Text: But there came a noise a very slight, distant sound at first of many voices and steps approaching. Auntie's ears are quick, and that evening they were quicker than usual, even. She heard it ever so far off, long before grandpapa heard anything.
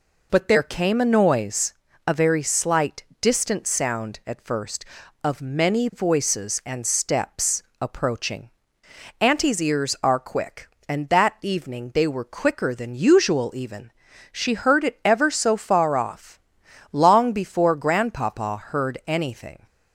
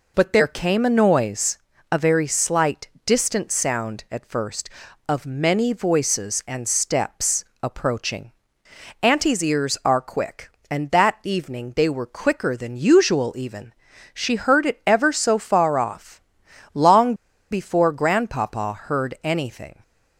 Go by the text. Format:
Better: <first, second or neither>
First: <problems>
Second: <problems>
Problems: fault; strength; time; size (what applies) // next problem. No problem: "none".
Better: first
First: pauses between "noise" and "a"; slight; at 1.7 s; 0.34 s long // pauses between "steps" and "approaching"; slight; at 7.6 s; 0.18 s long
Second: pauses between "noise" and "a"; slight; at 1.5 s; 0.34 s long // pauses between "steps" and "approaching"; slight; at 7.4 s; 0.18 s long // pauses between "long" and "before"; at 17.1 s; 0.37 s long